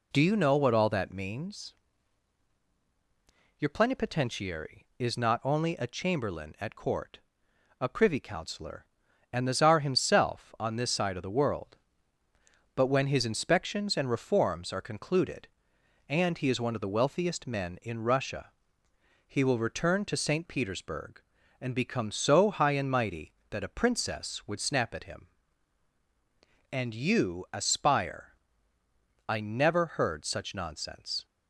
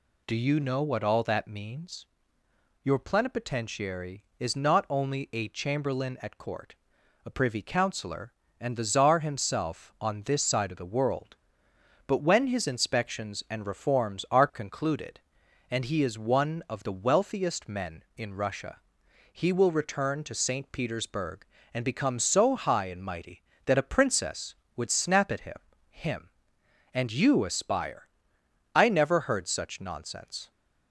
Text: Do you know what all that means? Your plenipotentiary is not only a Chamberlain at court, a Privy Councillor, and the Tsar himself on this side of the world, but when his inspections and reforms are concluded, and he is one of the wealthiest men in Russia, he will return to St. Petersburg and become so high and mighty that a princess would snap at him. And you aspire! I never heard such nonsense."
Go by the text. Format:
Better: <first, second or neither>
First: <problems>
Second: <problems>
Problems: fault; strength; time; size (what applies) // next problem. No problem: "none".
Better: first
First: none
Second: says "him" twice; at 25.8 s